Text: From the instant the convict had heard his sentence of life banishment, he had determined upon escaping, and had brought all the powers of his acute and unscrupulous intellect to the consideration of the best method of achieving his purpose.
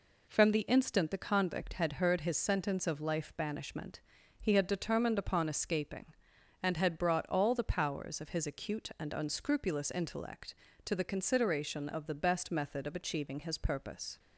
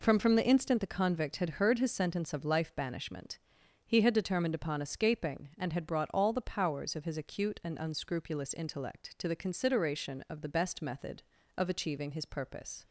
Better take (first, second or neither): first